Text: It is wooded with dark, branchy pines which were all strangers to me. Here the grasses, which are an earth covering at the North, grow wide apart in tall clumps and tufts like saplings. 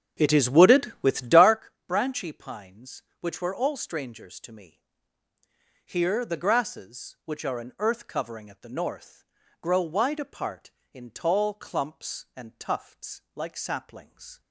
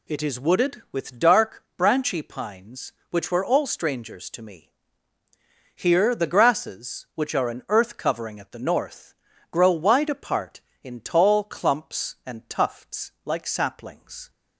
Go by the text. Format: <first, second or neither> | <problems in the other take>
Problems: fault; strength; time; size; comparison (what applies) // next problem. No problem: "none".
second | starts louder than the rest; strong; until 1.7 s; 7.5 dB